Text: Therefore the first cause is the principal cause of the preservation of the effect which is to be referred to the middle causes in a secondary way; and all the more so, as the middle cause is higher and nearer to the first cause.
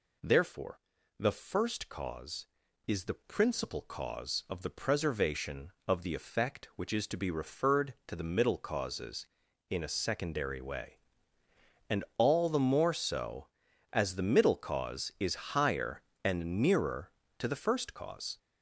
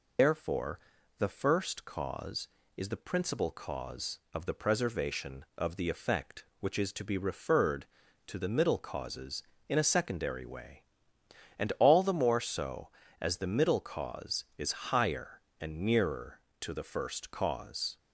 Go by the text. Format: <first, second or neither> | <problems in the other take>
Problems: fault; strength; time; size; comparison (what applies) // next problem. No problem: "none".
first | loses the start of "Therefore"; at 0.1 s; 110 ms // pauses between "Therefore" and "the"; at 0.7 s; 0.40 s long; also in the first